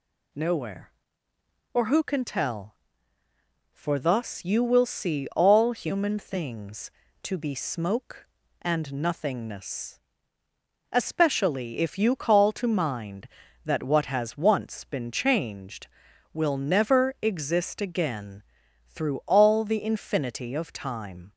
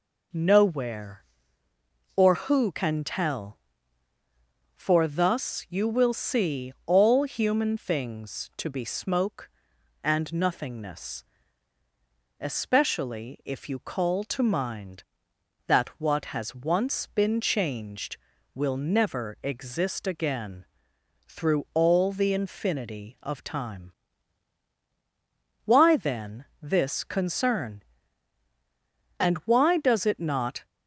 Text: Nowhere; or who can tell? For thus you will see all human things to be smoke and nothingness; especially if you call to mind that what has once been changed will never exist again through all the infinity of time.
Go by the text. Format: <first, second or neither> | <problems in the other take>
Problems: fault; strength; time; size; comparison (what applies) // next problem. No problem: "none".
first | pauses between "again" and "through"; noticeable; at 20.6 s; 0.62 s long; noticeable in the first // goes on to say "Why then this concern And why does it not"; strong; from 25.6 s on; 5.0 s long